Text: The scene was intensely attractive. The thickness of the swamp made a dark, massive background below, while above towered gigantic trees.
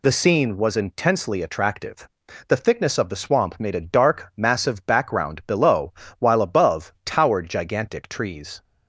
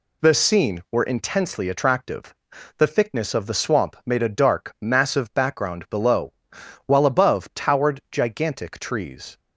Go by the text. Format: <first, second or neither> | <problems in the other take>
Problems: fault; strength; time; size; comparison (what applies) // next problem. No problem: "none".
first | says "were" for "was"; at 0.9 s